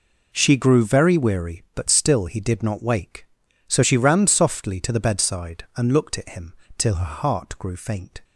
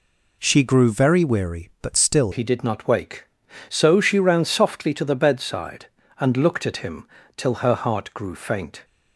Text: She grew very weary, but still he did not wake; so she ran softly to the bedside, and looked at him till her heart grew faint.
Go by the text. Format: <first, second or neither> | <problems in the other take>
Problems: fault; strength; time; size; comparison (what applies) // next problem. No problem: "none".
first | changes voice at "he"; from 2.3 s on; 6.5 s long // pauses between "him" and "till"; slight; at 7.0 s; 0.30 s long; slight in the first